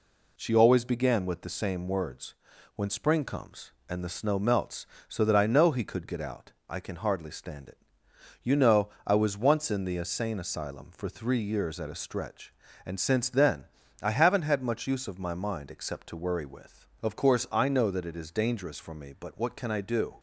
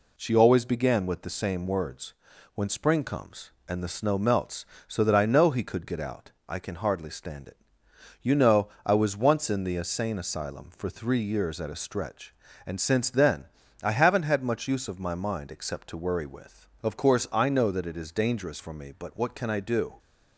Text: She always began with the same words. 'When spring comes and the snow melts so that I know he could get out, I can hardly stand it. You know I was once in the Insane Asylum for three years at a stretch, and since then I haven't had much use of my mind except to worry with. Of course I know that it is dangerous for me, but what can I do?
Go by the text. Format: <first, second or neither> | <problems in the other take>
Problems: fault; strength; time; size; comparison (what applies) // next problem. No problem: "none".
neither | pauses between "know" and "I"; slight; the same in both // pauses between "then" and "I"; slight; the same in both